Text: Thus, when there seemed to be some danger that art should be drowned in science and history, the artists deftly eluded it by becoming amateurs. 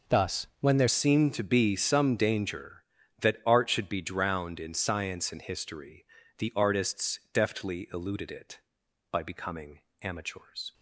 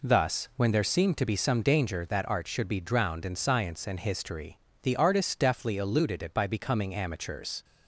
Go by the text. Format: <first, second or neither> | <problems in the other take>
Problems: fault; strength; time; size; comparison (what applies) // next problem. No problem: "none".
second | changes voice at "seemed"; from 0.8 s on; 9.9 s long // pauses between "becoming" and "amateurs"; slight; at 9.7 s; 0.22 s long